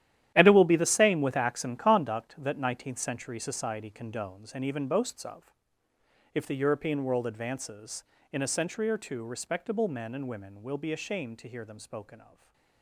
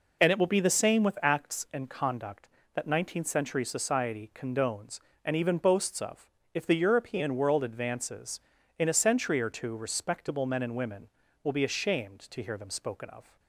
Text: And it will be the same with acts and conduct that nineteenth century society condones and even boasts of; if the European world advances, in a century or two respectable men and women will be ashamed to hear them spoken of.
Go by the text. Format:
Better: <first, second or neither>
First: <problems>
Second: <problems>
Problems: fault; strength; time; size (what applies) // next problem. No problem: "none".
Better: second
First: gets quieter; strong; throughout; 14 dB // stays silent after the last word; slight; from 12.2 s on; 0.6 s long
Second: none